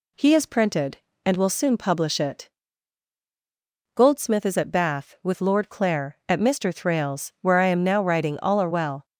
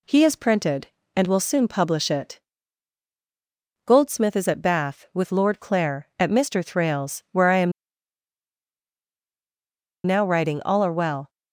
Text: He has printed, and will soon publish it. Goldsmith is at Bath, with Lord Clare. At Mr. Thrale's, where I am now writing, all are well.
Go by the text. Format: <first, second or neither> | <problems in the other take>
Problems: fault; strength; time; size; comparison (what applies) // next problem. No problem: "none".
first | pauses between "am" and "now"; strong; at 7.7 s; 2.3 s long